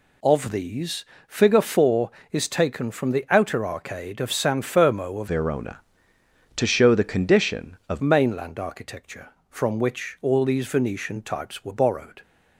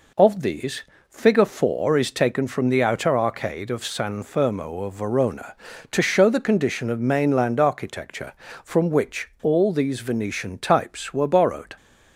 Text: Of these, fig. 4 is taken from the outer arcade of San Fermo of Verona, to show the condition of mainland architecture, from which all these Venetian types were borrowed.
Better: second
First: changes voice from "Verona" to "of"; from 5.2 to 8.0 s; 2.8 s long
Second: none

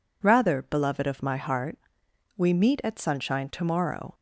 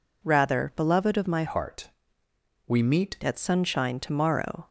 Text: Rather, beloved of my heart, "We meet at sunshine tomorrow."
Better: first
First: none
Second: changes voice from "heart" to "meet"; from 1.4 to 3.1 s; 1.7 s long

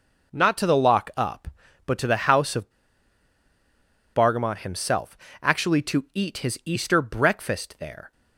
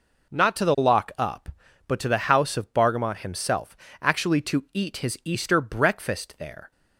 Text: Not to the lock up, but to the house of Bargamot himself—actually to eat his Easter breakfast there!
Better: second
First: pauses between "of" and "Bargamot"; strong; at 2.7 s; 1.4 s long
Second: none

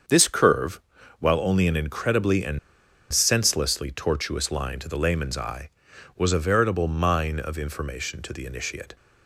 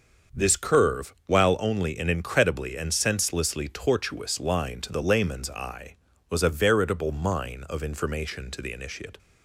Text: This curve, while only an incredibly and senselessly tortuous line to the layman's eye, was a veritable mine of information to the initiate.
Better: second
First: starts louder than the rest; until 1.4 s; 7 dB // pauses between "and" and "senselessly"; noticeable; at 2.5 s; 0.54 s long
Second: starts louder than the rest; until 1.4 s; 6.5 dB

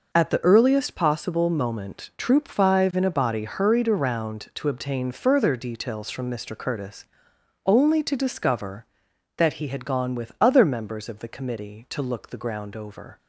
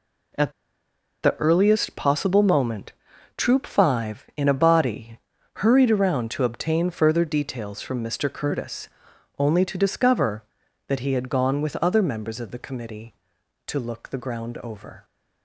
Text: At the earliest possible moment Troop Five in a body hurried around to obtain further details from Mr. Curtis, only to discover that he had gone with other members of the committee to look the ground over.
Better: first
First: none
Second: pauses between "At" and "the"; noticeable; at 0.5 s; 0.71 s long // pauses between "moment" and "Troop"; at 2.9 s; 0.44 s long // pauses between "body" and "hurried"; at 5.1 s; 0.38 s long

